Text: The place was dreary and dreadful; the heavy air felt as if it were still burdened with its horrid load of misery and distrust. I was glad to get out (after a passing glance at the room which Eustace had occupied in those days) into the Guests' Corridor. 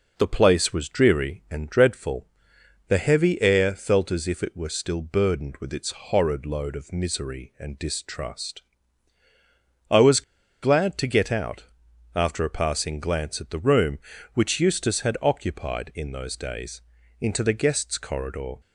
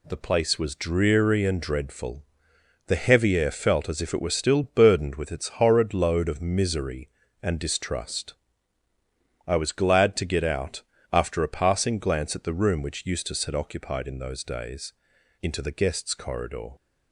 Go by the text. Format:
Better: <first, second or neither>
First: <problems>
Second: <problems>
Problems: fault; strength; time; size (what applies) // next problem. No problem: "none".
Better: second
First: pauses between "was" and "glad"; at 10.2 s; 0.40 s long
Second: none